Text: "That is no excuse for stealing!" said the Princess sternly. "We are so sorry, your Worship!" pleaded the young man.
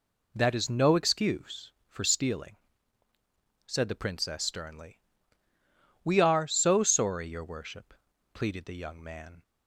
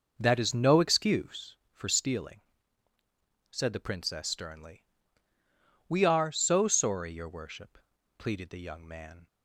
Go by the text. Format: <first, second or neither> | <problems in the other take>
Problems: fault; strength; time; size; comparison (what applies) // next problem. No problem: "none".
first | starts louder than the rest; noticeable; until 1.5 s; 5.5 dB